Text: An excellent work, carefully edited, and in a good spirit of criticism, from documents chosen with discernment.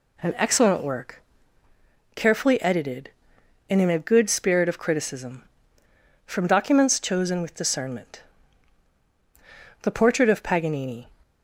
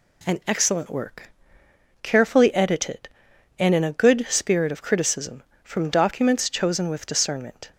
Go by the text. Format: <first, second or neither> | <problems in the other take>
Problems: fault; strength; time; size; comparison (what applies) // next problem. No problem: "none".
second | goes on to say "The portrait of Paganini"; noticeable; from 9.8 s on; 1.2 s long